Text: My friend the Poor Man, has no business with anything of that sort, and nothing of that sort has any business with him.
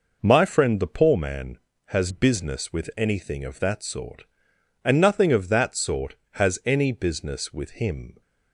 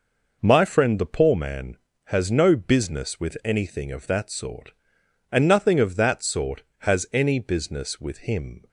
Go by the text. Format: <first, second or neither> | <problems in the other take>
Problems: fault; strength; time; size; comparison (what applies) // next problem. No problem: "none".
second | skips "no"; at 2.1 s